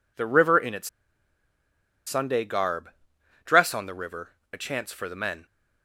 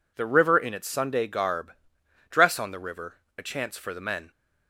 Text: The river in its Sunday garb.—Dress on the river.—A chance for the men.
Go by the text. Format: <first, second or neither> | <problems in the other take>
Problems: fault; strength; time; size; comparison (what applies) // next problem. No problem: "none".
second | pauses between "its" and "Sunday"; at 0.8 s; 1.1 s long